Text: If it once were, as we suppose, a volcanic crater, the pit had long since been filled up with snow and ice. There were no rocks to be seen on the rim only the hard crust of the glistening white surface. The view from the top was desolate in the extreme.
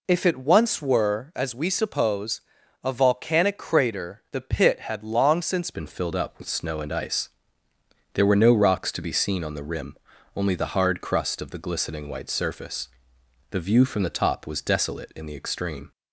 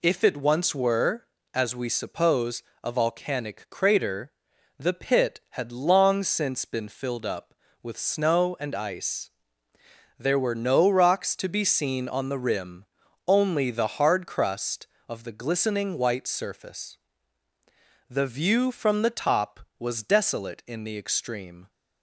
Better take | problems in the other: second | changes voice at "been"; from 5.7 s on; 10.2 s long // pauses between "rim" and "only"; at 9.9 s; 0.38 s long; also in the second

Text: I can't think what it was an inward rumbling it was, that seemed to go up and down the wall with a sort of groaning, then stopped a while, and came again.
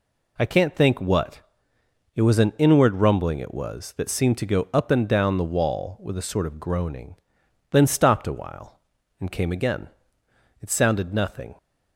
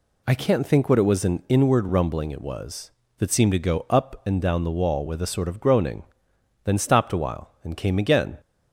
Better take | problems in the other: second | pauses between "what" and "it"; noticeable; at 1.4 s; 0.74 s long // goes on to say "It sounded nothing"; noticeable; from 10.6 s on; 0.96 s long

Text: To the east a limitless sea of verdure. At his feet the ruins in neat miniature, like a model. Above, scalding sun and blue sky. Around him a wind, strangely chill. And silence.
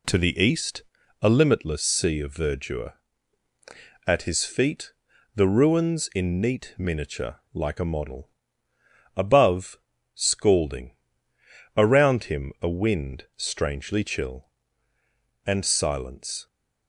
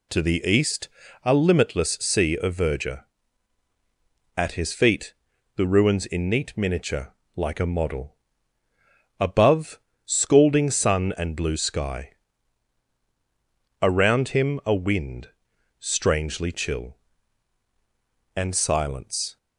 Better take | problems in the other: second | pauses between "east" and "a"; at 0.8 s; 0.40 s long; slight in the second // pauses between "feet" and "the"; at 4.9 s; 0.42 s long; also in the second // skips "sun and blue sky"; at 11.3 s

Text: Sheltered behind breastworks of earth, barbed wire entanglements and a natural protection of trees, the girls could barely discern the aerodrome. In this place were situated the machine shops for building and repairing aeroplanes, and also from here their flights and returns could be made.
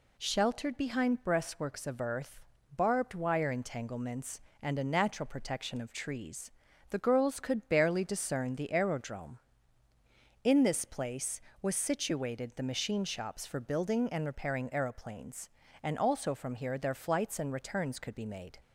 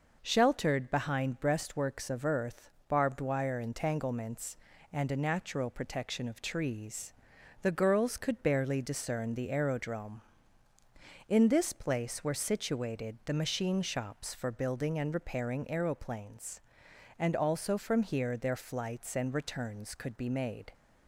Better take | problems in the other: second | says "was" for "were"; at 11.6 s

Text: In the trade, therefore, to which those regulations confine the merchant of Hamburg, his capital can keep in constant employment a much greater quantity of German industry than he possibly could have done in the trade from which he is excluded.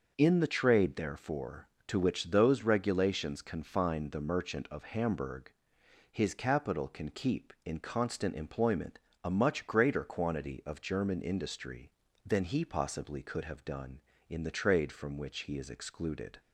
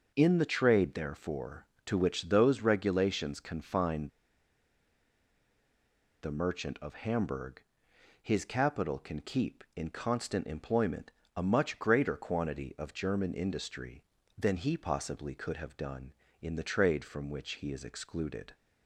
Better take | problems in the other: first | starts louder than the rest; noticeable; until 1.1 s; 6 dB; noticeable in the first // pauses between "confine" and "the"; strong; at 4.0 s; 2.1 s long // pauses between "employment" and "a"; slight; at 11.1 s; 0.26 s long; slight in the first

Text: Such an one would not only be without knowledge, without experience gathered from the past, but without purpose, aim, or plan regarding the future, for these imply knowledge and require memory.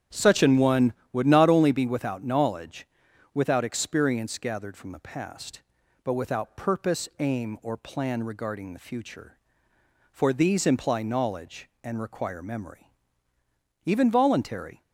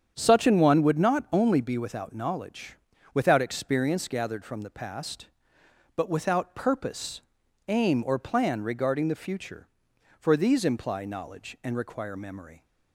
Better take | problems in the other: second | starts louder than the rest; strong; until 1.3 s; 10 dB; strong in the second // goes on to say "Even voluntary"; noticeable; from 13.8 s on; 0.96 s long

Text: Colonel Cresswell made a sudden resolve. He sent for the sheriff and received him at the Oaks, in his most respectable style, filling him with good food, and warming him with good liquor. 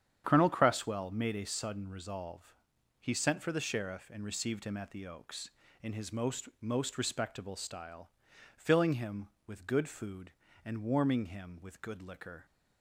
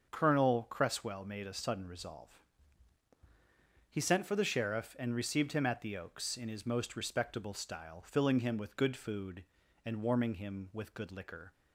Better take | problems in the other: second | starts louder than the rest; strong; until 1.2 s; 8.5 dB; also in the second // says "most" twice; at 6.5 s

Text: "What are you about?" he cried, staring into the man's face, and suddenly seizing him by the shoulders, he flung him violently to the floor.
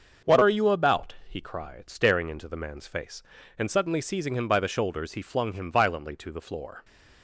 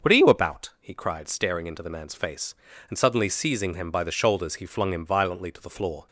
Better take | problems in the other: neither | starts louder than the rest; the same in both

